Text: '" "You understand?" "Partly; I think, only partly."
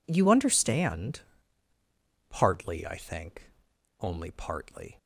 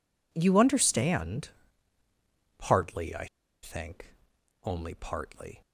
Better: first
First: none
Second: pauses between "I" and "think"; at 3.2 s; 0.36 s long

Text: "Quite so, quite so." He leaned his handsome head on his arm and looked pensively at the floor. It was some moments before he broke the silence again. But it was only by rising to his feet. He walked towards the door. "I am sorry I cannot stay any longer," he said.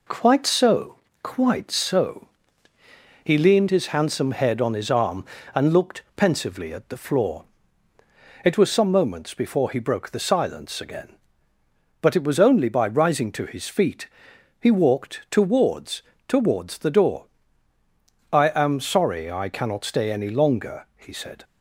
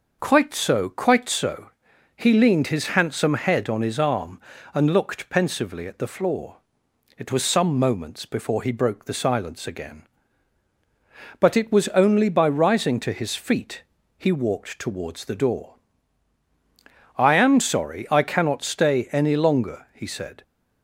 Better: second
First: says "towards" twice; at 16.2 s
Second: none

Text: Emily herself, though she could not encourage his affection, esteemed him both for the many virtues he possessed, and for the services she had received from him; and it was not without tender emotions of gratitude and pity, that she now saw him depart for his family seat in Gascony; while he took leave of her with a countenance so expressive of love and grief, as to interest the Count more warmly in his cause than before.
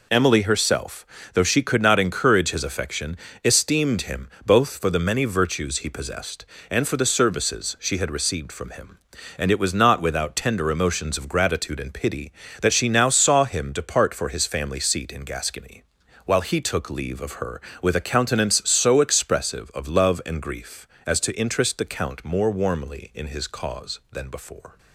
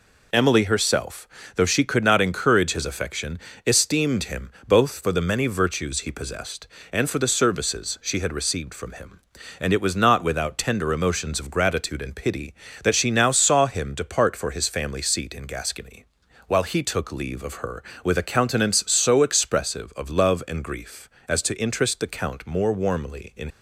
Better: first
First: pauses between "him" and "both"; slight; at 4.2 s; 0.18 s long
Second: pauses between "him" and "both"; slight; at 4.4 s; 0.18 s long // stops before "his cause than before"; at 23.4 s

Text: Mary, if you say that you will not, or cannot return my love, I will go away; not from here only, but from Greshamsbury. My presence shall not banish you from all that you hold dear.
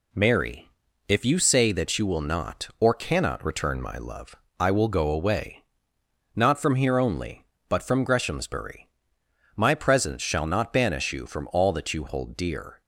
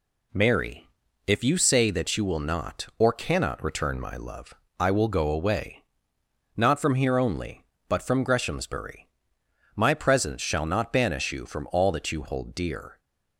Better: neither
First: none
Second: none

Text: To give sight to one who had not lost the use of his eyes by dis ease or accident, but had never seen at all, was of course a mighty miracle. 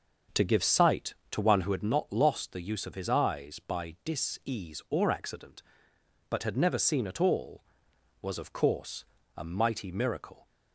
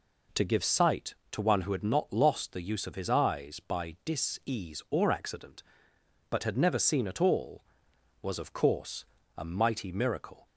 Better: second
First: starts louder than the rest; until 1.9 s; 6.5 dB // pauses between "course" and "a"; slight; at 9.0 s; 0.32 s long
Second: pauses between "course" and "a"; slight; at 9.0 s; 0.32 s long

